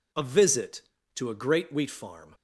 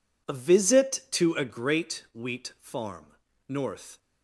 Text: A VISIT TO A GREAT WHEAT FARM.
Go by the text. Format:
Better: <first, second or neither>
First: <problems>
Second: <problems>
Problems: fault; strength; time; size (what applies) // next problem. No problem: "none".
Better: first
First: none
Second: goes on to say "NORTH"; from 3.4 s on; 0.52 s long